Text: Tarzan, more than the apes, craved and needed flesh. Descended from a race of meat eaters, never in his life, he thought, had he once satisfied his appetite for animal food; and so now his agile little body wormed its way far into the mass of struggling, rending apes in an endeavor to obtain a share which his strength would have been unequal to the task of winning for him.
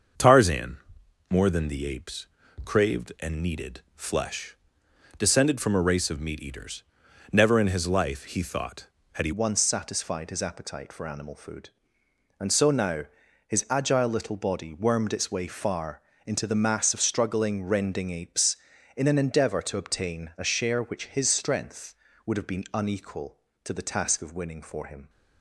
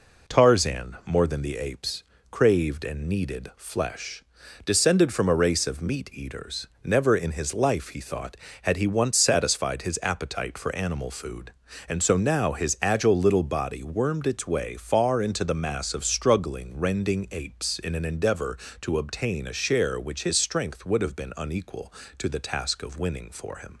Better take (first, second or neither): second